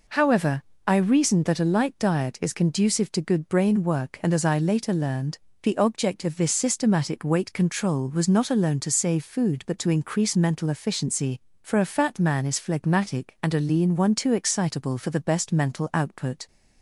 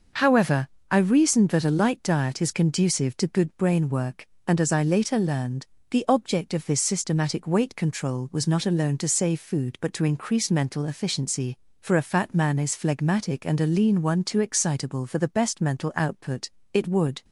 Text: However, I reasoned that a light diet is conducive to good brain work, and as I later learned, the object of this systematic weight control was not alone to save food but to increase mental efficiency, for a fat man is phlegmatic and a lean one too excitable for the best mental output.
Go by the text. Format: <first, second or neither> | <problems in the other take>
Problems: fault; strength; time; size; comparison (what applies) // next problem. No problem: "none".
first | goes on to say "It would"; from 16.7 s on; 0.52 s long